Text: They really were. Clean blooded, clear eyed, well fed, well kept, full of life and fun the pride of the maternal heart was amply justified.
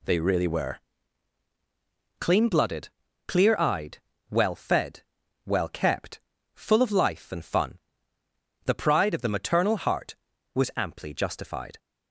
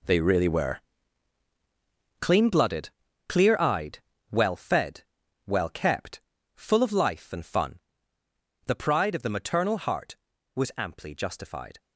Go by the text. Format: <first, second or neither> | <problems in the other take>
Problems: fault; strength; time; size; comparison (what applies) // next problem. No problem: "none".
first | gets quieter; strong; throughout; 13 dB // pauses between "fun" and "the"; noticeable; at 7.7 s; 0.88 s long; noticeable in the first